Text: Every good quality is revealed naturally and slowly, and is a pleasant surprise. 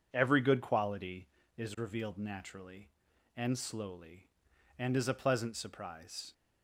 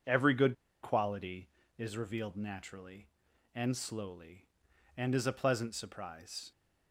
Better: first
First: none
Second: pauses between "good" and "quality"; slight; at 0.5 s; 0.28 s long

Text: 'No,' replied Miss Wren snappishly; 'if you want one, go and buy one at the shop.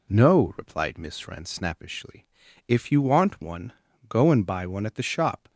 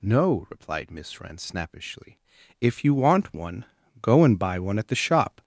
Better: first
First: none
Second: gets louder; strong; throughout; 7 dB

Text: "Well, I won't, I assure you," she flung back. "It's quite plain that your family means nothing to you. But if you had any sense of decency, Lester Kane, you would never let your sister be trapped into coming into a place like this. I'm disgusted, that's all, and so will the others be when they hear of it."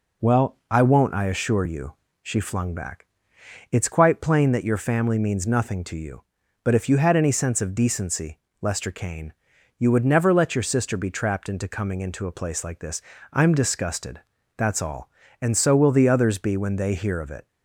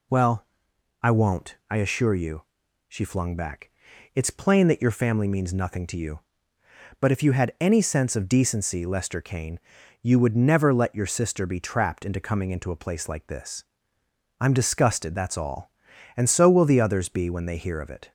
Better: first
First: none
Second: skips "quite"; at 4.2 s

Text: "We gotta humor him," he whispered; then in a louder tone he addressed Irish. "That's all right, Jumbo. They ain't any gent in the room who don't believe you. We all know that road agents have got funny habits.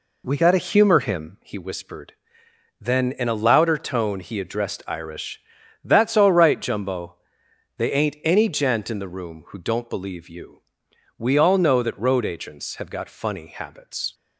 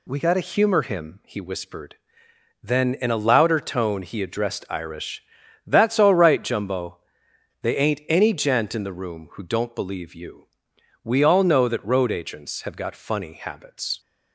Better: second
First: starts louder than the rest; slight; until 1.4 s; 3 dB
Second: none

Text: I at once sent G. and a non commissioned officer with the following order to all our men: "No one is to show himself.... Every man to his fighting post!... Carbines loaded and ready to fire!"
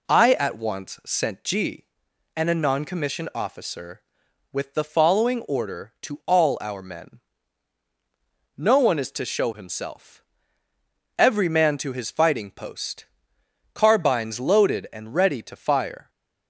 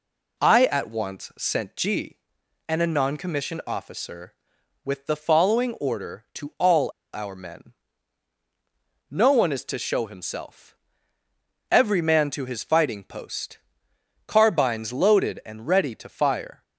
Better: first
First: none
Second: pauses between "all" and "our"; slight; at 6.8 s; 0.25 s long

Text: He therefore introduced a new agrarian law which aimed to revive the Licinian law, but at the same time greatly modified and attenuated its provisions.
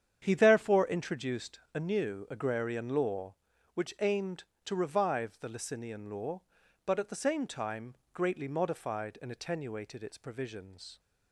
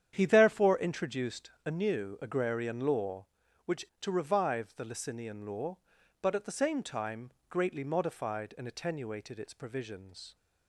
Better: first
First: starts louder than the rest; strong; until 1.2 s; 8.5 dB // pauses between "introduced" and "a"; slight; at 1.5 s; 0.16 s long // pauses between "time" and "greatly"; slight; at 7.9 s; 0.18 s long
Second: starts louder than the rest; strong; until 1.1 s; 9 dB // pauses between "introduced" and "a"; slight; at 1.5 s; 0.16 s long // skips "aimed"; at 3.9 s // pauses between "time" and "greatly"; slight; at 7.3 s; 0.18 s long

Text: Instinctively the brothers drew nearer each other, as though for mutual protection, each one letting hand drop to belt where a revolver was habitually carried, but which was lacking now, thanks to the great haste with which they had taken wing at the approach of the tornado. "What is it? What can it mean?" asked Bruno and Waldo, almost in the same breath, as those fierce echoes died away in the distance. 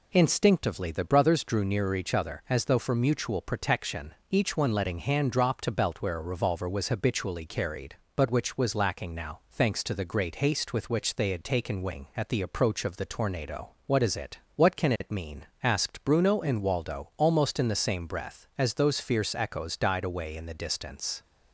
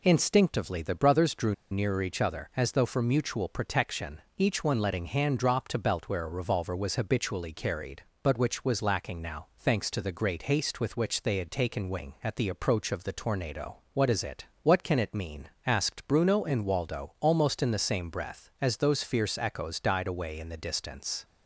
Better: first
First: none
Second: pauses between "drew" and "nearer"; slight; at 1.5 s; 0.16 s long

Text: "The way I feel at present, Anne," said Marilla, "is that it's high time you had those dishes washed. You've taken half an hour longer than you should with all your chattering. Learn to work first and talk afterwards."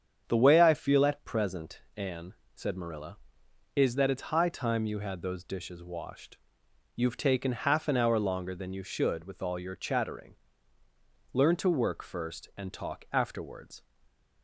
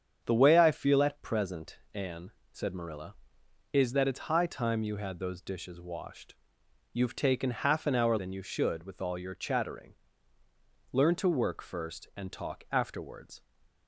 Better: first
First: starts louder than the rest; strong; until 1.2 s; 8 dB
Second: starts louder than the rest; strong; until 1.2 s; 7.5 dB // skips "longer"; at 8.1 s

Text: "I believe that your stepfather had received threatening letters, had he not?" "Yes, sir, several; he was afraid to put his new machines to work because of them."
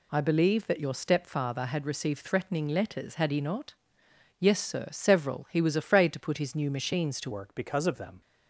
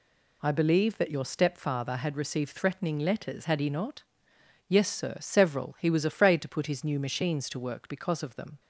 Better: second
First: changes voice at "work"; from 7.3 s on; 0.9 s long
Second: none

